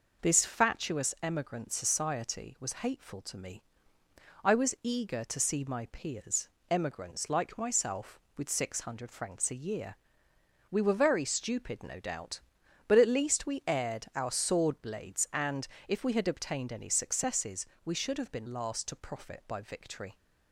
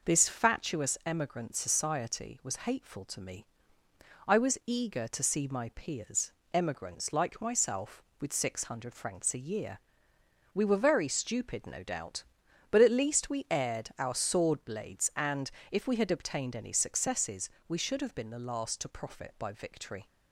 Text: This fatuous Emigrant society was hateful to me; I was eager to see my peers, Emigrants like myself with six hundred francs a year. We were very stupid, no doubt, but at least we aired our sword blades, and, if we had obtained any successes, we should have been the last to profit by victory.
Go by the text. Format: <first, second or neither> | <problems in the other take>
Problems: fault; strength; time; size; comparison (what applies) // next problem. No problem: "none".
second | skips "the"; at 18.4 s